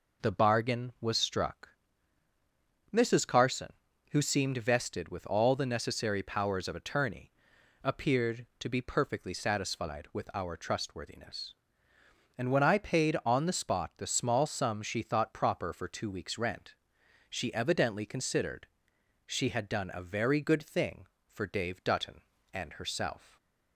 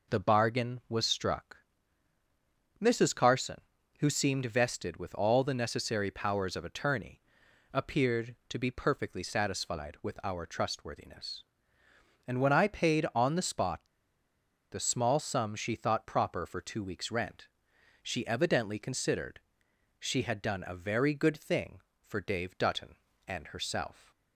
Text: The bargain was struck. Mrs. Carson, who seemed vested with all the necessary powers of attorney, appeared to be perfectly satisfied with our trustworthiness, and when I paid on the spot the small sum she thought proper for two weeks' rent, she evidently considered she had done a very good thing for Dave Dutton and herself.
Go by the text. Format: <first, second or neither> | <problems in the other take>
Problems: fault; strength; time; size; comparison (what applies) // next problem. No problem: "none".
first | pauses between "spot" and "the"; noticeable; at 13.8 s; 0.90 s long // pauses between "considered" and "she"; noticeable; at 19.3 s; 0.60 s long; noticeable in the first